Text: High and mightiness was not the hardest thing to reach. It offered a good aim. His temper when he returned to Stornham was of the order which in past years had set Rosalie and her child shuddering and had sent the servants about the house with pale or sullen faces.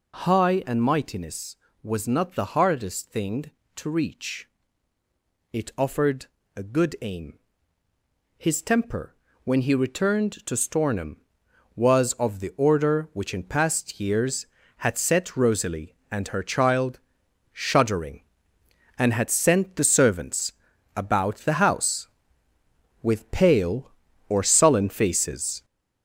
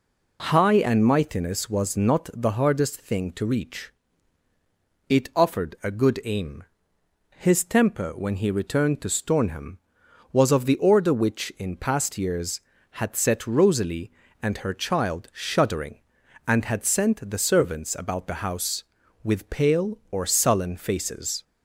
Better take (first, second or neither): second